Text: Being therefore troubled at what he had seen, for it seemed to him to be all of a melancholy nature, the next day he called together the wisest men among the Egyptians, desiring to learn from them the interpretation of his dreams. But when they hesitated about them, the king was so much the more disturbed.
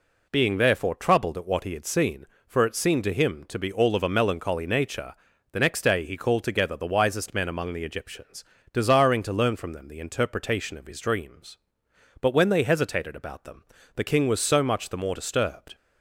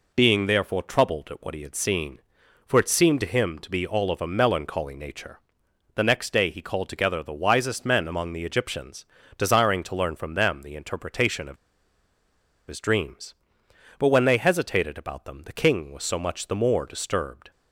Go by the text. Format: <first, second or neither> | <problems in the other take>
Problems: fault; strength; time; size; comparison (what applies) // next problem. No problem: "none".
first | pauses between "of" and "his"; at 11.5 s; 1.1 s long